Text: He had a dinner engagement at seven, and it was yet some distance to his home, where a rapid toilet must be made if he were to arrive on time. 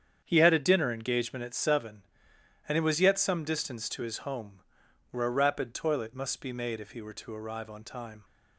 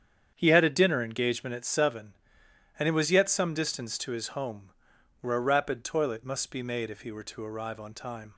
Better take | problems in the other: neither | starts louder than the rest; strong; the same in both

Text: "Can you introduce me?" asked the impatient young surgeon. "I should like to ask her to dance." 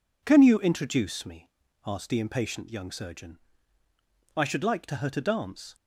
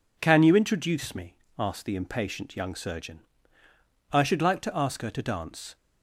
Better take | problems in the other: second | skips "ask"; at 4.9 s

